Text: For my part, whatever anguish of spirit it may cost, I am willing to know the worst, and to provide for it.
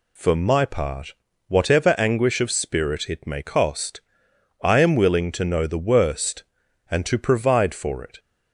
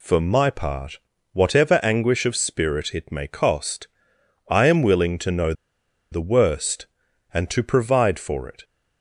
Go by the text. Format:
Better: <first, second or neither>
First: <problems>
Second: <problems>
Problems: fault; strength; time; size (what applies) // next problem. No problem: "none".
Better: first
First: none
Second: pauses between "know" and "the"; noticeable; at 5.5 s; 0.58 s long